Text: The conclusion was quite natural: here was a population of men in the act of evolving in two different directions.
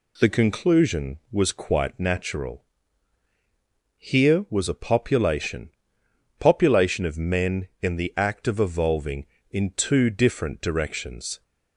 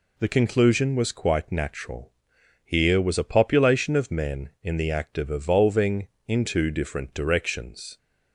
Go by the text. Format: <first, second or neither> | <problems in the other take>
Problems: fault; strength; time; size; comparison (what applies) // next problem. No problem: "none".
second | says "population" twice; at 6.3 s